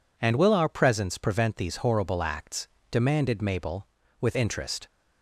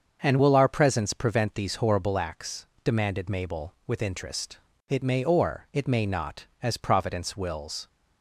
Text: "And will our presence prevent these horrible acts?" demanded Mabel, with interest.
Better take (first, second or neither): first